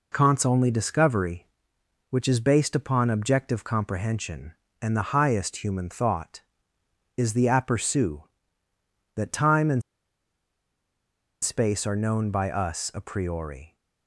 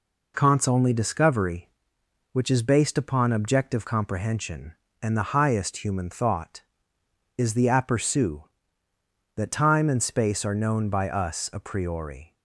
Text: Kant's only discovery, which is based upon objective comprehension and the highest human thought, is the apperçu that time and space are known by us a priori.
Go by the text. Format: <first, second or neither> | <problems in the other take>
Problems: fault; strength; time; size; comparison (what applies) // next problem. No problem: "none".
second | pauses between "and" and "space"; strong; at 9.8 s; 1.6 s long